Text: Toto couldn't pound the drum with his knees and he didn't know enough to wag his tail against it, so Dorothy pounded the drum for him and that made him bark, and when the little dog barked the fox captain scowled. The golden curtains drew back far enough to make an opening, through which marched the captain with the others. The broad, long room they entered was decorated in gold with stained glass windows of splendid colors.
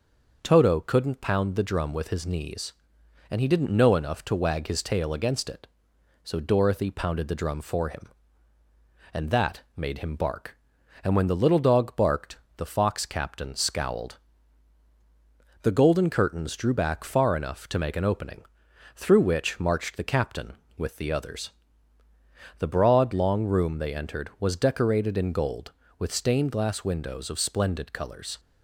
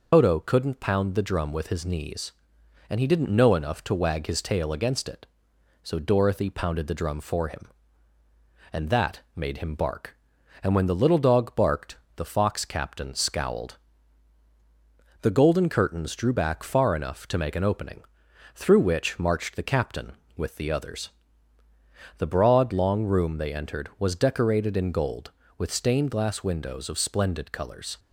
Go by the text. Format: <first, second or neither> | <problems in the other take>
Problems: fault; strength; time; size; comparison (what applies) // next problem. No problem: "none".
first | loses the start of "Toto"; at 0.1 s; 115 ms // pauses between "barked" and "the"; slight; at 11.9 s; 0.20 s long; slight in the first